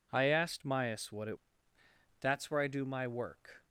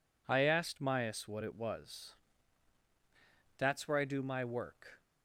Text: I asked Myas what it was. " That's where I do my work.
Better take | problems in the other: second | skips "was"; at 1.3 s

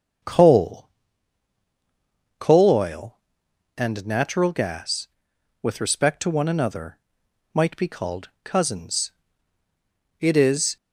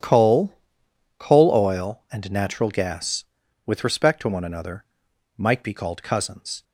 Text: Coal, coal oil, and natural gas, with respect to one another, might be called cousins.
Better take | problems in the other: second | starts louder than the rest; until 2.7 s; 7 dB // pauses between "called" and "cousins"; slight; at 8.2 s; 0.16 s long // goes on to say "It is"; from 10.2 s on; 0.56 s long

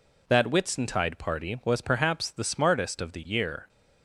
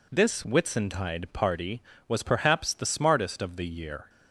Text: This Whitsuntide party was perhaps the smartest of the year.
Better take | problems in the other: second | says "That" for "This"; at 0.2 s

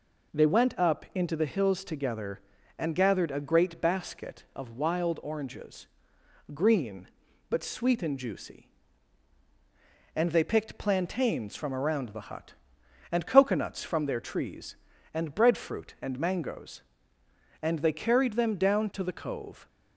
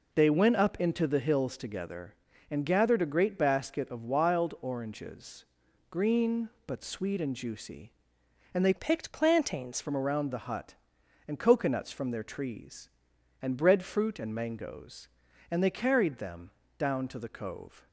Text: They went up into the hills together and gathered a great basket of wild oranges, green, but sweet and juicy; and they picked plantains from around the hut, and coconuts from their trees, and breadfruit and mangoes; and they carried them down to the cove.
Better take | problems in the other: first | changes voice from "picked" to "plantains"; from 8.7 to 9.7 s; 1.0 s long // pauses between "them" and "down"; slight; at 16.4 s; 0.30 s long

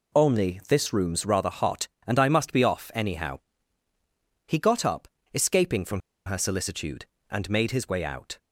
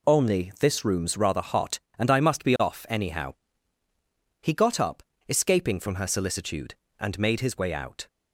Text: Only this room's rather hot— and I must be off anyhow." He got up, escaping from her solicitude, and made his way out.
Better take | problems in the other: second | pauses between "from" and "her"; slight; at 6.0 s; 0.25 s long

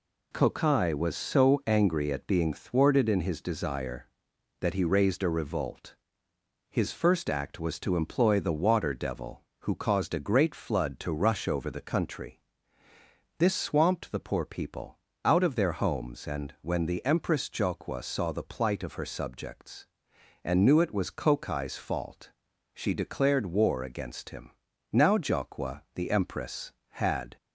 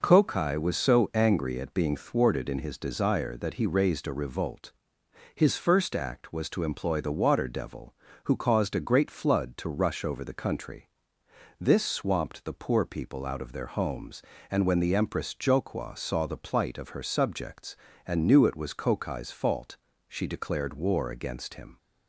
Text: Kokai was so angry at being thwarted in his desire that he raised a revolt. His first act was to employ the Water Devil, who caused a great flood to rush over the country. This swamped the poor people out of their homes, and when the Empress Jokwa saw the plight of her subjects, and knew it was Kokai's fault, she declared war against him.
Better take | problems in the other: second | pauses between "people" and "out"; slight; at 14.9 s; 0.28 s long // goes on to say "Now Jokwa the Empress had"; strong; from 24.9 s on; 2.4 s long

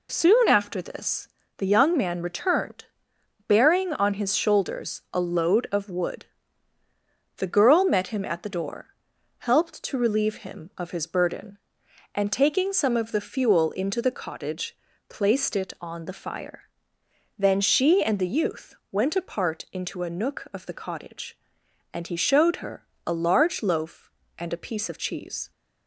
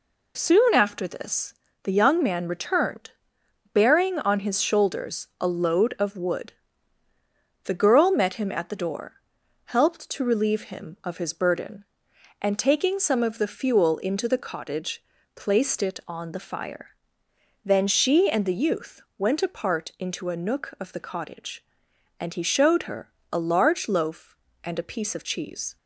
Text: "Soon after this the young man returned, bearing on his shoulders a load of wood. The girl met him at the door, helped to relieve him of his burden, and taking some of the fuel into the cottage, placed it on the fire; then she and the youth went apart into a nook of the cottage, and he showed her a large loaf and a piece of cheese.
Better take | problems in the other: neither | pauses between "this" and "the"; slight; the same in both // pauses between "youth" and "went"; slight; the same in both // pauses between "her" and "a"; slight; the same in both

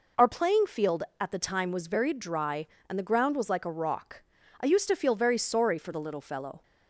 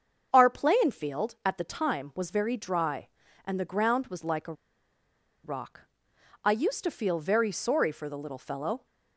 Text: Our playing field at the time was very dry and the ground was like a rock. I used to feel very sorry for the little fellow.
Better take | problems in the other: first | starts louder than the rest; until 1.3 s; 7 dB // pauses between "a" and "rock"; noticeable; at 4.5 s; 0.90 s long

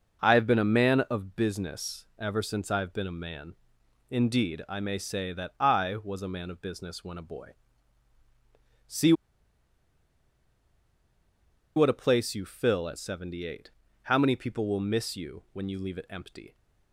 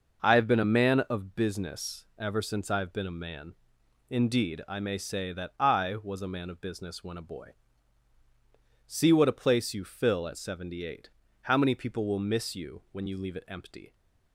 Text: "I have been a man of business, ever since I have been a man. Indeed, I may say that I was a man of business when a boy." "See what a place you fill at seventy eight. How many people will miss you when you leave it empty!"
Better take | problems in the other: second | pauses between "See" and "what"; strong; at 9.1 s; 2.6 s long

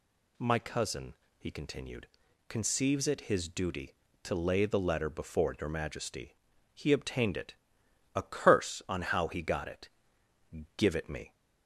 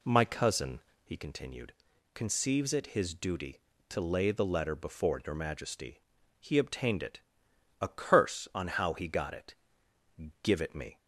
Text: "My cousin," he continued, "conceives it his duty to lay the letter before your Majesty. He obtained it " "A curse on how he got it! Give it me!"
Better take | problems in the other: first | starts louder than the rest; slight; until 1.1 s; 2 dB

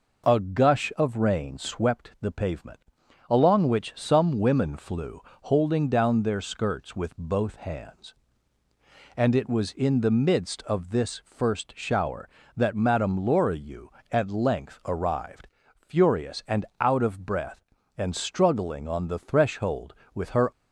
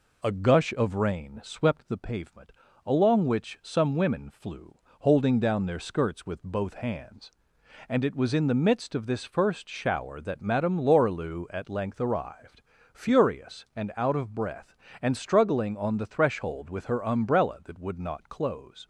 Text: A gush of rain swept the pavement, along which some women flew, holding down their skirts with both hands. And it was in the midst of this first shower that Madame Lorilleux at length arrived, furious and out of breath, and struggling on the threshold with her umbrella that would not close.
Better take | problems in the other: second | pauses between "and" and "out"; slight; at 16.6 s; 0.16 s long // stops before "umbrella that would not close"; at 20.5 s

